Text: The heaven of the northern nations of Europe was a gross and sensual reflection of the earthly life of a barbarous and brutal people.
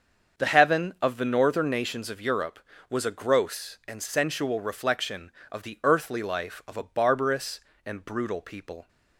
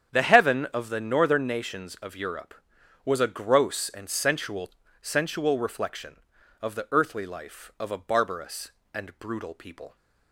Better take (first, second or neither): first